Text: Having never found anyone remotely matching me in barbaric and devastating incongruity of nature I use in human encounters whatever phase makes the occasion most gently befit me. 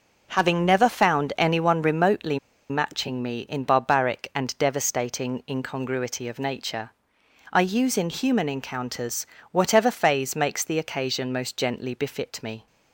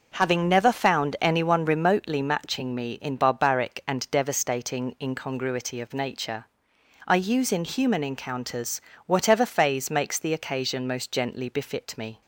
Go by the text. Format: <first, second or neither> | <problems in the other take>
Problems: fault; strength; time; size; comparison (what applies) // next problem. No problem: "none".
second | pauses between "remotely" and "matching"; slight; at 2.3 s; 0.32 s long // pauses between "nature" and "I"; noticeable; at 6.9 s; 0.60 s long; noticeable in the second // pauses between "encounters" and "whatever"; slight; at 9.2 s; 0.28 s long; slight in the second